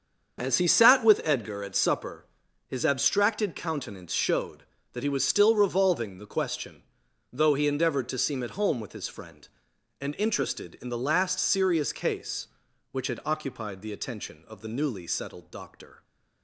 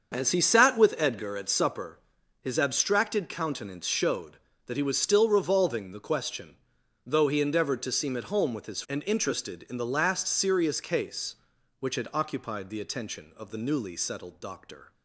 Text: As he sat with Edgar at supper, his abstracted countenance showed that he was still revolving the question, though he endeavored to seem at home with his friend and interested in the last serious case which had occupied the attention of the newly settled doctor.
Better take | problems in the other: first | starts louder than the rest; until 1.1 s; 6.5 dB; also in the first // skips "friend"; at 8.8 s

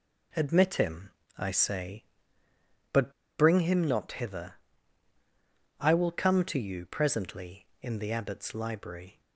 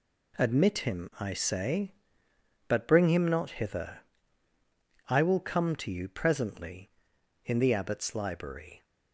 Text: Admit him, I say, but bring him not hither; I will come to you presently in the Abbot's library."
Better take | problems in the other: second | pauses between "but" and "bring"; slight; at 3.1 s; 0.27 s long

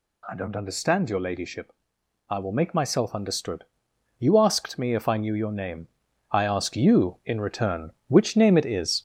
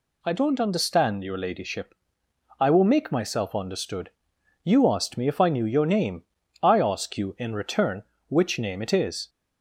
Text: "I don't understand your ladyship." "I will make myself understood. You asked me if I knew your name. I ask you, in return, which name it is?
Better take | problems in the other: second | gets louder; noticeable; throughout; 4.5 dB

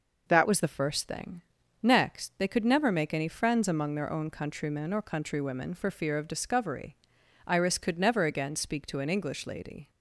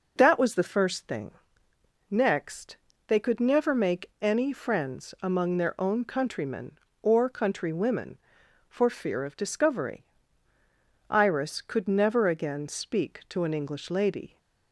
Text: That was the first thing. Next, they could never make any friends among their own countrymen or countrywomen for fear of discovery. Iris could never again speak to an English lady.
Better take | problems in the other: second | changes voice at "was"; from 0.4 s on; 9.4 s long

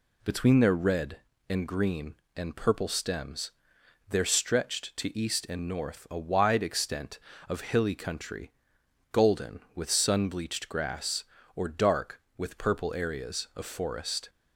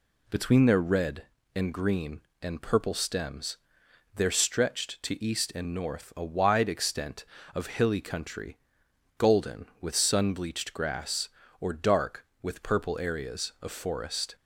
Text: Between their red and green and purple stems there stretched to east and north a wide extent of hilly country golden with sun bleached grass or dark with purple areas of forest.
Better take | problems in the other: neither | pauses between "stems" and "there"; noticeable; the same in both // pauses between "country" and "golden"; noticeable; the same in both

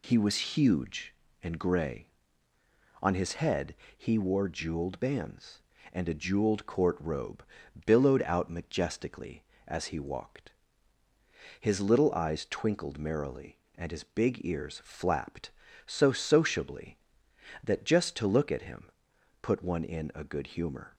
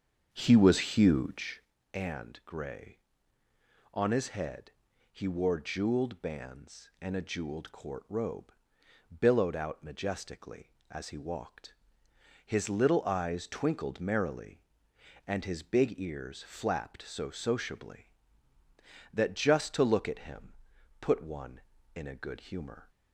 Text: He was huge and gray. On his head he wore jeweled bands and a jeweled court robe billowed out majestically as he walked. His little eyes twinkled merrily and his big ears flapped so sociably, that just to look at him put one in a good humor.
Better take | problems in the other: first | starts louder than the rest; until 1.8 s; 7 dB // pauses between "head" and "he"; at 4.7 s; 0.40 s long; slight in the first // pauses between "robe" and "billowed"; noticeable; at 8.5 s; 0.68 s long; also in the first // pauses between "him" and "put"; noticeable; at 20.5 s; 0.46 s long; noticeable in the first

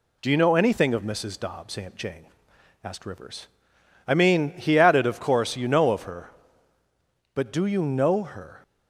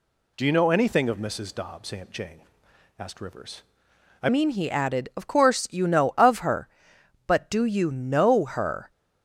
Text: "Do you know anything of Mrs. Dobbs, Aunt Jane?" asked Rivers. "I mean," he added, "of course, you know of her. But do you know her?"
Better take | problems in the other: first | changes voice at "mean"; from 4.3 s on; 4.6 s long

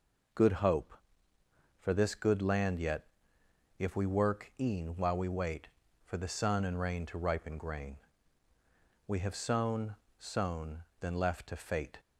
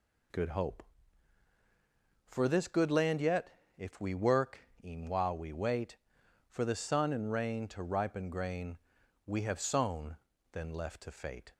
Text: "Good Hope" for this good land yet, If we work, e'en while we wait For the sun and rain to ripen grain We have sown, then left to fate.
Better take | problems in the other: second | pauses between "grain" and "We"; at 7.9 s; 1.1 s long; noticeable in the second // says "sown" twice; at 10.1 s

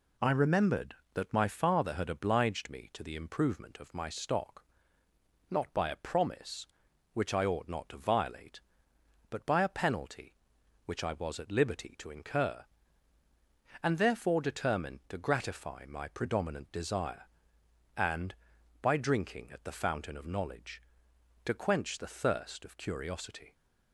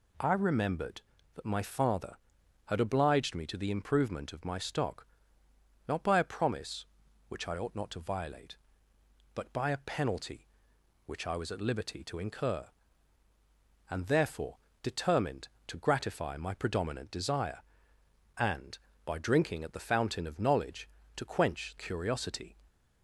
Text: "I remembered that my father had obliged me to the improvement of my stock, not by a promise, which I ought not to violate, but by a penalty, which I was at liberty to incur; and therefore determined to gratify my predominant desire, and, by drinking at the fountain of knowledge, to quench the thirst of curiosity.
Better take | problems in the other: first | pauses between "therefore" and "determined"; slight; at 14.5 s; 0.24 s long // skips "the thirst of"; at 21.7 s

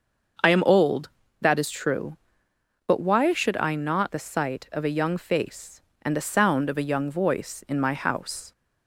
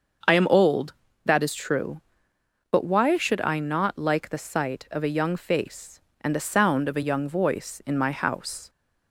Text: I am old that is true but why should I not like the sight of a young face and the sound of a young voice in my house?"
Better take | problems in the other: second | starts louder than the rest; until 1.7 s; 6.5 dB; also in the second // skips "like"; at 4.1 s

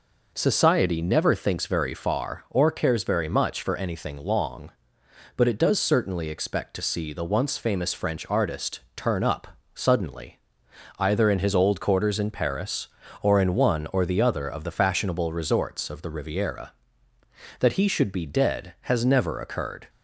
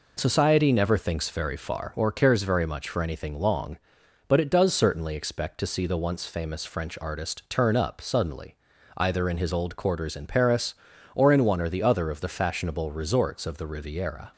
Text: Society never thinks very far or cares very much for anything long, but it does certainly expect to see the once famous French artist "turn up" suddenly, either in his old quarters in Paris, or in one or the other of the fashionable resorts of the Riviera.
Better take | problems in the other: second | pauses between "artist" and "turn"; slight; at 8.7 s; 0.16 s long // pauses between "up" and "suddenly"; slight; at 9.4 s; 0.28 s long // goes on to say "That he should be dead has never occurred"; strong; from 17.5 s on; 2.3 s long

